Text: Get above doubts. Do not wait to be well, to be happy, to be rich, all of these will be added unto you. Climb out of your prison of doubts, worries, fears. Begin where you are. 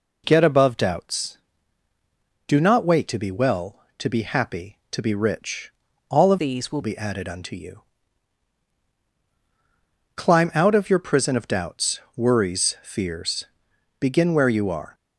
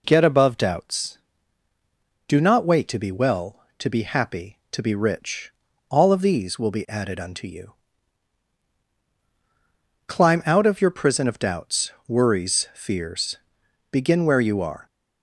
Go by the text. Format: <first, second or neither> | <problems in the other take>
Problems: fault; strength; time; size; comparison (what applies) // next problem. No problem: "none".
second | changes voice from "these" to "will"; from 6.3 to 6.8 s; 0.5 s long